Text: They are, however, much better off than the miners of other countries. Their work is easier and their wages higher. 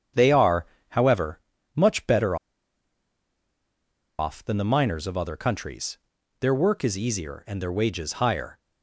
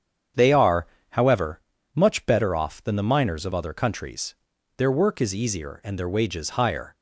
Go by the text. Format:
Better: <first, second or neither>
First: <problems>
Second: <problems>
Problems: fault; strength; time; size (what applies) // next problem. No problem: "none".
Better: second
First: starts louder than the rest; strong; until 1.4 s; 8 dB // pauses between "better" and "off"; strong; at 2.3 s; 1.8 s long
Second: starts louder than the rest; strong; until 1.6 s; 8 dB